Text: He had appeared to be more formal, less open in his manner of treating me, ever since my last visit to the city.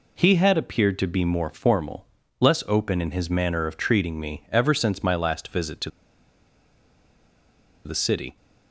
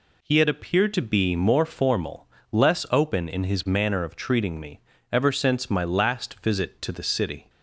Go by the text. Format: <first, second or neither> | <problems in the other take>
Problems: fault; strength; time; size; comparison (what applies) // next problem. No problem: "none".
second | pauses between "to" and "the"; strong; at 5.9 s; 1.9 s long